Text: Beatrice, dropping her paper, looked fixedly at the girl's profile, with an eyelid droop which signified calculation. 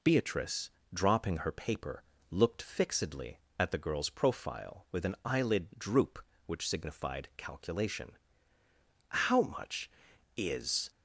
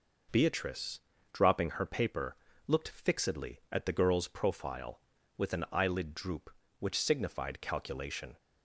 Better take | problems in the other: second | goes on to say "How much is"; strong; from 9.0 s on; 1.8 s long

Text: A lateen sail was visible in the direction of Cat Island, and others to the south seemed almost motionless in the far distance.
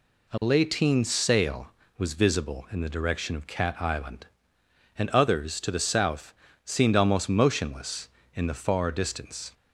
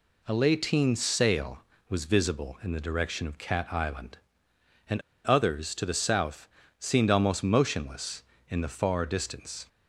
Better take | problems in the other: first | pauses between "and" and "others"; slight; at 5.0 s; 0.23 s long // pauses between "south" and "seemed"; slight; at 6.4 s; 0.30 s long; slight in the first

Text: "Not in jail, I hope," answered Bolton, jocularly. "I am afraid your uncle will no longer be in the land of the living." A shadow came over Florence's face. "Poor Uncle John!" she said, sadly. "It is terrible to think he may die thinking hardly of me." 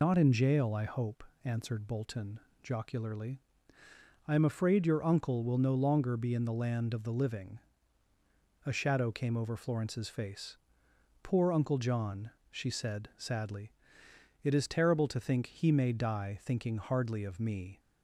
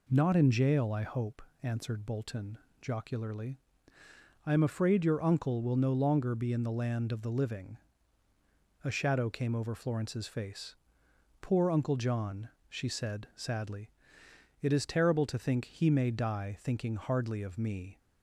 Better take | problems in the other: second | loses the start of "Not"; at 0.0 s; 105 ms

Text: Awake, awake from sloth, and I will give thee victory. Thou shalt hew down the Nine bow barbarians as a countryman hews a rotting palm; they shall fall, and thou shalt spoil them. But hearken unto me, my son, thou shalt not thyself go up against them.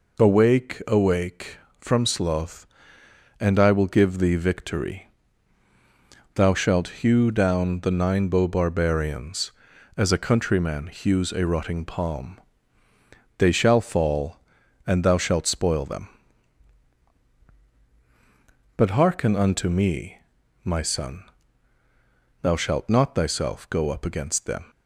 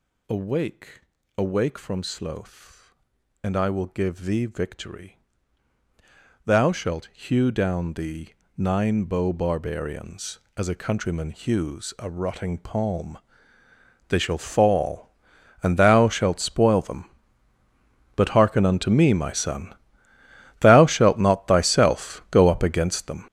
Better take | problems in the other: first | gets louder; strong; throughout; 13 dB // pauses between "the" and "Nine"; slight; at 8.3 s; 0.26 s long

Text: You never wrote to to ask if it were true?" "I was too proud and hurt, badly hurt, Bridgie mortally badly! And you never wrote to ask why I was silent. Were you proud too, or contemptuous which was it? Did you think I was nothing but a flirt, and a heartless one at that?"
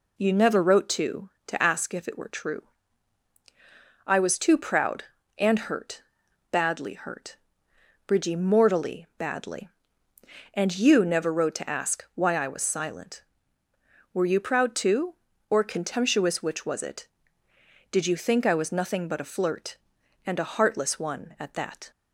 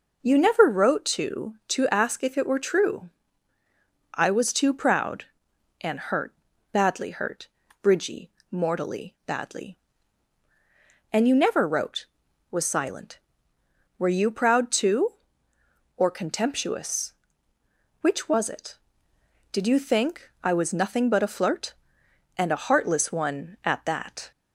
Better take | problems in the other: first | pauses between "Bridgie" and "mortally"; slight; at 8.2 s; 0.22 s long // skips "to ask why I"; at 12.2 s

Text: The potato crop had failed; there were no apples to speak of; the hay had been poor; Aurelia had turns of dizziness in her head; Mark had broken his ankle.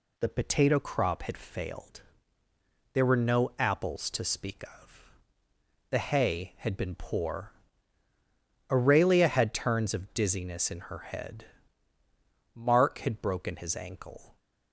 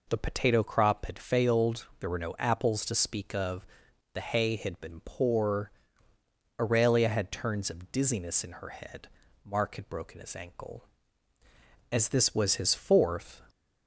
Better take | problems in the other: first | goes on to say "As this was his fourth"; from 11.9 s on; 1.5 s long

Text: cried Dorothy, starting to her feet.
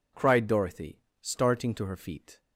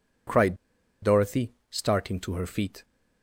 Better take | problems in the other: first | pauses between "cried" and "Dorothy"; noticeable; at 0.5 s; 0.47 s long

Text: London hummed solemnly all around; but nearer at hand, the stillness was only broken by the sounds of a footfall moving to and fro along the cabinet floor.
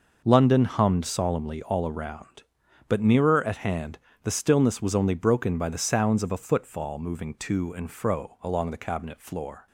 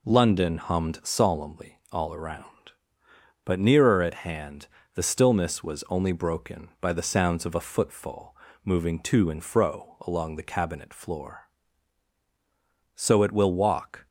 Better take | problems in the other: first | pauses between "footfall" and "moving"; slight; at 8.3 s; 0.30 s long // goes on to say "So it will walk"; noticeable; from 12.9 s on; 1.1 s long

